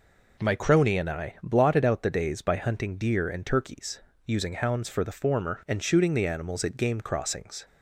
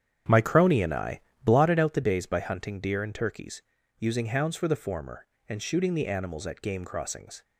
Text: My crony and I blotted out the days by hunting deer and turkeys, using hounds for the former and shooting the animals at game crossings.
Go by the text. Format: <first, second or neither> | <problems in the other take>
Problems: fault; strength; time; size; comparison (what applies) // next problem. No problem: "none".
first | starts louder than the rest; strong; until 1.7 s; 9 dB // pauses between "I" and "blotted"; slight; at 1.2 s; 0.24 s long